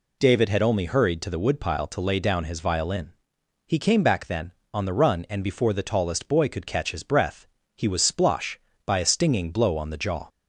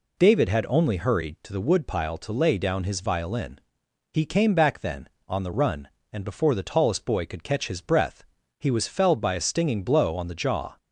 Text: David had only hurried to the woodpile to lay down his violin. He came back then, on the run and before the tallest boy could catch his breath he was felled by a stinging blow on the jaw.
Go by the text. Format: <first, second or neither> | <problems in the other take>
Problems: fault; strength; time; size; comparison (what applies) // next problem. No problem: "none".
second | pauses between "breath" and "he"; slight; at 7.4 s; 0.30 s long; slight in the second // says "splosh" for "felled"; at 8.1 s